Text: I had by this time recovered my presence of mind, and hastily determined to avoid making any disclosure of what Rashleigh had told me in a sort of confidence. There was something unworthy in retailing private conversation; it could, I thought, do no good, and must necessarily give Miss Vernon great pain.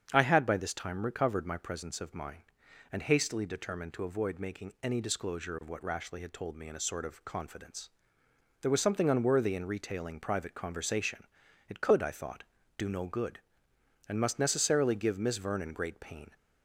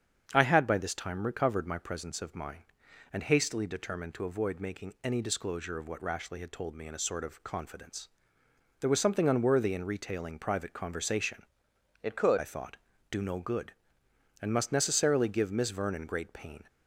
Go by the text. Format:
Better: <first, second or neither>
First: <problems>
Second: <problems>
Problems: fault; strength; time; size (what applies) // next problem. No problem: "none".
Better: first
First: starts louder than the rest; strong; until 1.1 s; 7.5 dB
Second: starts louder than the rest; strong; until 1.3 s; 7.5 dB // changes voice from "it" to "could"; from 12.0 to 12.3 s; 0.3 s long